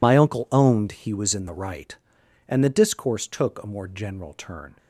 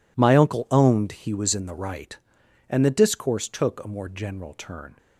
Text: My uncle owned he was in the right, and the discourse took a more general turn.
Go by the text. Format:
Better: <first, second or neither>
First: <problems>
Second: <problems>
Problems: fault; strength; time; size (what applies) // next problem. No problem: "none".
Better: second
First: loses the start of "My"; at 0.0 s; 55 ms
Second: none